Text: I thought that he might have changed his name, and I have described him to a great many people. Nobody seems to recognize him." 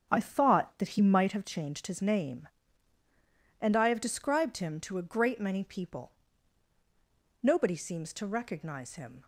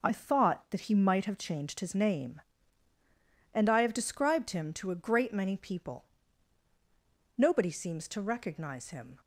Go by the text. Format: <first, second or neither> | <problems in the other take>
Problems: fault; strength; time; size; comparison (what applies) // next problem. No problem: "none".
second | starts louder than the rest; until 1.4 s; 6.5 dB